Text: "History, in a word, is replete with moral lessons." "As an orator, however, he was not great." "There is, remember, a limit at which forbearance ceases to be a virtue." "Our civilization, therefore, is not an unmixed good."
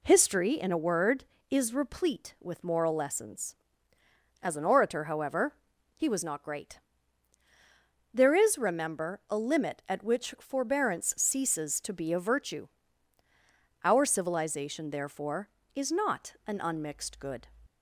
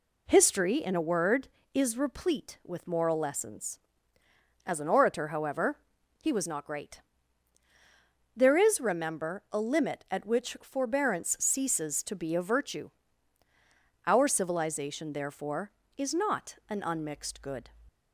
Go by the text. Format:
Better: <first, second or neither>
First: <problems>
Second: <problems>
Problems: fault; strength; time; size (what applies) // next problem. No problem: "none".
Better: neither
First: none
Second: none